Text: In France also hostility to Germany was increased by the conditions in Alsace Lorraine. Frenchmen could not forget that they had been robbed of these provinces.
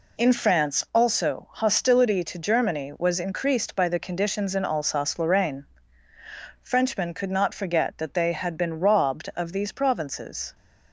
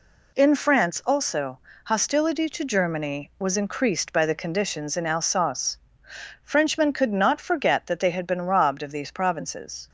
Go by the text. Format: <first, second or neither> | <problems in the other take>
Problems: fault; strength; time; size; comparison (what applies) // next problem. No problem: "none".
first | pauses between "also" and "hostility"; slight; at 1.5 s; 0.26 s long // skips "Lorraine"; at 6.0 s